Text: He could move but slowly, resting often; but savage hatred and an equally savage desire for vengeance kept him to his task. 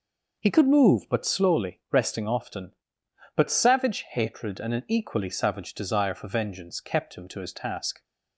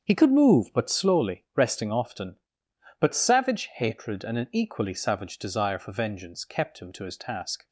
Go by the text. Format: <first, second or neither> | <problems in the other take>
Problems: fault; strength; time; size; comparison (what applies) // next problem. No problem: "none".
first | gets quieter; strong; throughout; 9.5 dB